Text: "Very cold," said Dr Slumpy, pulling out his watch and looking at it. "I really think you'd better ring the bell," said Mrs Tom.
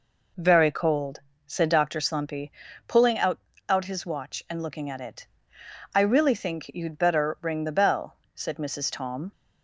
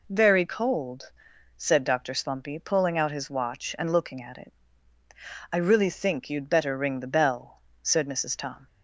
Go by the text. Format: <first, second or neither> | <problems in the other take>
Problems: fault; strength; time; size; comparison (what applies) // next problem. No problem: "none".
second | says "out" twice; at 3.6 s